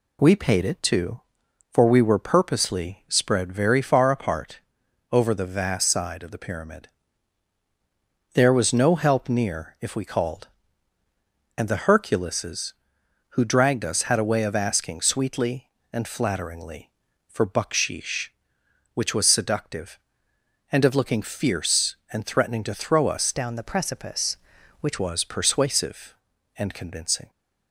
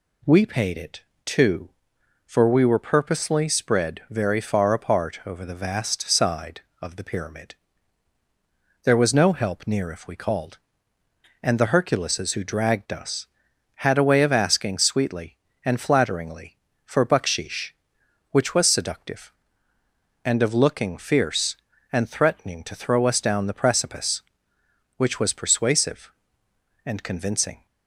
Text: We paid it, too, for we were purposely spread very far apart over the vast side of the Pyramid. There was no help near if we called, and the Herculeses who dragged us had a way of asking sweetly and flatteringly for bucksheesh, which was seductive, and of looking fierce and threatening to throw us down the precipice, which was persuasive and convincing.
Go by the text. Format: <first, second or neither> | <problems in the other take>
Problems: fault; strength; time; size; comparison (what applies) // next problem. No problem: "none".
second | pauses between "apart" and "over"; noticeable; at 4.6 s; 0.50 s long // changes voice from "down" to "which"; from 23.3 to 24.9 s; 1.6 s long